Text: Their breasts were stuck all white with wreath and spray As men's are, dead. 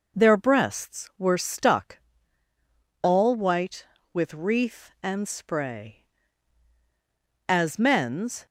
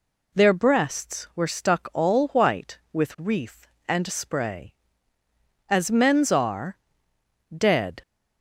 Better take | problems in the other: second | pauses between "stuck" and "all"; at 1.9 s; 1.0 s long // stops before "are dead"; at 8.4 s

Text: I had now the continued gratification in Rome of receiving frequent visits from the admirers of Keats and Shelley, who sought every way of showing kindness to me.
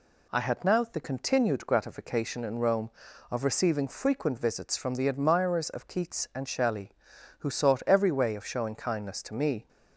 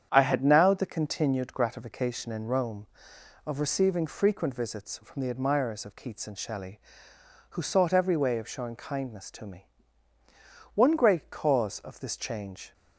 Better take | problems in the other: first | starts louder than the rest; strong; until 1.1 s; 8 dB // goes on to say "One great cause of this change"; strong; from 10.7 s on; 2.0 s long

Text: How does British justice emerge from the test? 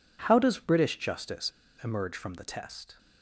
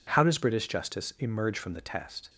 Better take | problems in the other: second | pauses between "justice" and "emerge"; slight; at 1.4 s; 0.31 s long

